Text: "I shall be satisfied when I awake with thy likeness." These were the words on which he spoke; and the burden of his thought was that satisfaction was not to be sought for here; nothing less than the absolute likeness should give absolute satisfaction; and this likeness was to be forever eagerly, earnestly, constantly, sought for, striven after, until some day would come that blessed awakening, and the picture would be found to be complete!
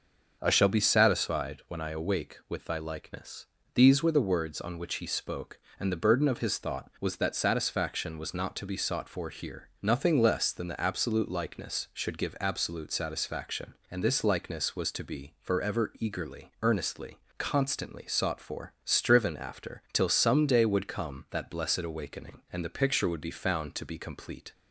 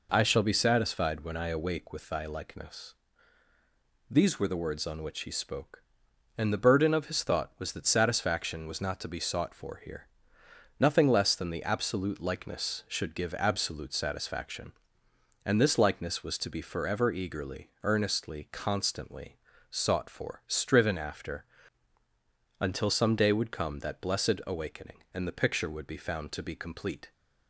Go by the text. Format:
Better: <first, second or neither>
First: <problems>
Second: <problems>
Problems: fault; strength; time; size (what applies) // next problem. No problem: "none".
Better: second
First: starts louder than the rest; noticeable; until 1.4 s; 6 dB // says "till" for "until"; at 19.9 s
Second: none